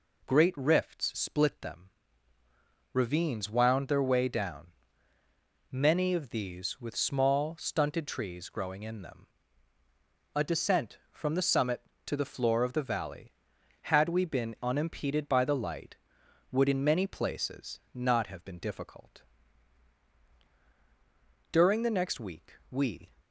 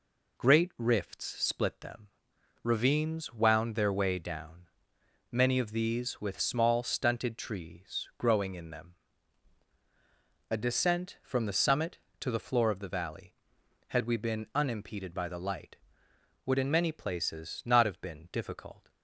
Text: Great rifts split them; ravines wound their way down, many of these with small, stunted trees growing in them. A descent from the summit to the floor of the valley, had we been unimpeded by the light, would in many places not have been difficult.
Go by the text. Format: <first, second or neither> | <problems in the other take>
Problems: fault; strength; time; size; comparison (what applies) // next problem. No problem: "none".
second | goes on to say "During the next week we"; from 21.5 s on; 1.6 s long